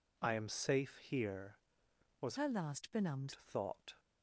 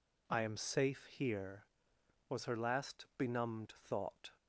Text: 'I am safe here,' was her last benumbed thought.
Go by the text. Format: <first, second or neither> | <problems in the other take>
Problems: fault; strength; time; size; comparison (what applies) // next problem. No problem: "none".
second | changes voice from "her" to "benumbed"; from 2.3 to 3.3 s; 1.0 s long